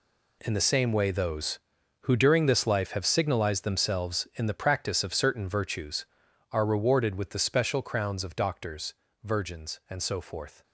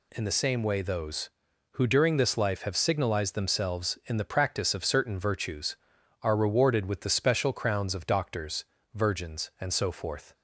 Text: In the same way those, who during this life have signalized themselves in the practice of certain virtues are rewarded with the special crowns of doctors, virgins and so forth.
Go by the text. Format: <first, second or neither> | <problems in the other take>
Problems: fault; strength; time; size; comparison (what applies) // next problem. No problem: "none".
second | gets quieter; strong; throughout; 12.5 dB